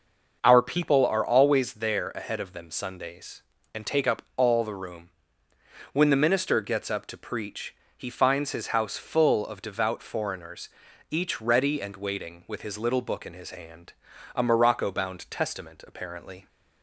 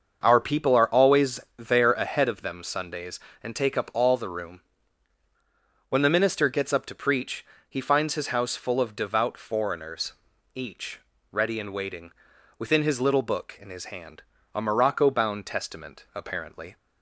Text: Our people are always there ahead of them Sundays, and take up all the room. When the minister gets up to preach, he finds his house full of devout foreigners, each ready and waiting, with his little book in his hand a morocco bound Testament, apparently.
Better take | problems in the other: first | starts louder than the rest; until 1.2 s; 6.5 dB; noticeable in the first // pauses between "always" and "there"; slight; at 1.4 s; 0.16 s long // pauses between "each" and "ready"; slight; at 10.9 s; 0.32 s long // says "within" for "with"; at 12.5 s // pauses between "hand" and "a"; slight; at 14.2 s; 0.32 s long; also in the first

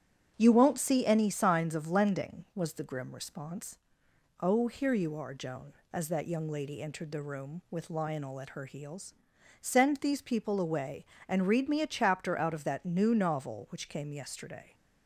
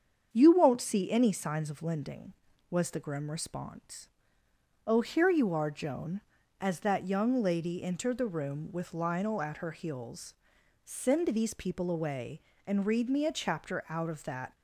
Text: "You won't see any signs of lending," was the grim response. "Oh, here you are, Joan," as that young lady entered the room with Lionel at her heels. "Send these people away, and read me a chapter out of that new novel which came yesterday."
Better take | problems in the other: first | starts louder than the rest; strong; until 1.3 s; 7.5 dB; strong in the first // stops before "new novel which came yesterday"; at 14.5 s

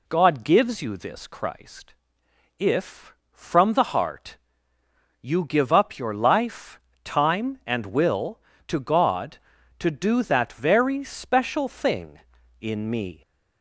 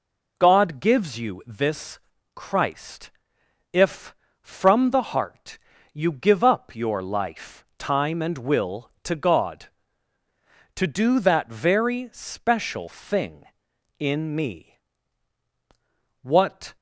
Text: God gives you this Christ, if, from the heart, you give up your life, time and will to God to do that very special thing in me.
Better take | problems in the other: first | pauses between "this" and "Christ"; slight; at 1.9 s; 0.36 s long // goes on to say "What"; from 16.2 s on; 0.54 s long

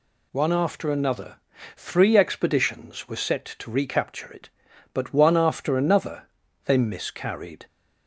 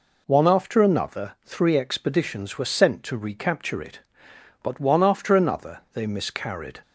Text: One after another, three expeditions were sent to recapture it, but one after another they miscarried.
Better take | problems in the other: second | says "set" for "sent"; at 3.1 s // pauses between "another" and "they"; at 6.2 s; 0.38 s long

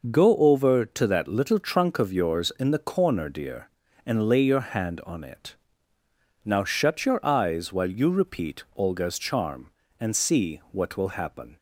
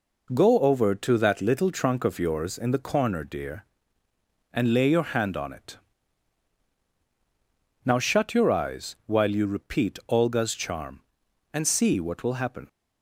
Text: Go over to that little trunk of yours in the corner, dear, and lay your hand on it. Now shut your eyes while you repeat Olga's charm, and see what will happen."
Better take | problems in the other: neither | none

